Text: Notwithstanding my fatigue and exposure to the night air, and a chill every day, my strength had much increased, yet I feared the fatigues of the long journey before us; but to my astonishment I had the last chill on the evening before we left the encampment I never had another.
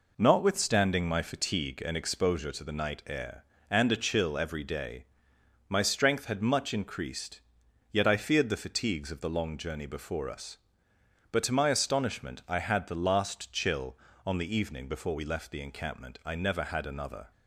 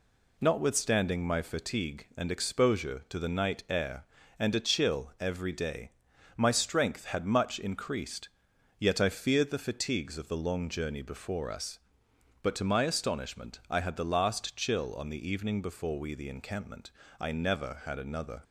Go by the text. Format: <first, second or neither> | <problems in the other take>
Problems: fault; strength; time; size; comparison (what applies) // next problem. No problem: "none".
first | skips "left"; at 16.1 s // pauses between "encampment" and "I"; slight; at 16.9 s; 0.28 s long